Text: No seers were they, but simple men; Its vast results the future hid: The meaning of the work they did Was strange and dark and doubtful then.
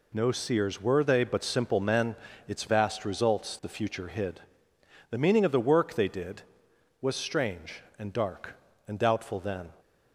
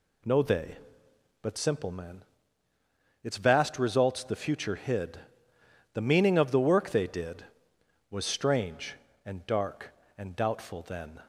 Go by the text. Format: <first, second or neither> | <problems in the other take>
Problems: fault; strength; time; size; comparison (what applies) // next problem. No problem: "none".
first | skips "seers were"; at 0.4 s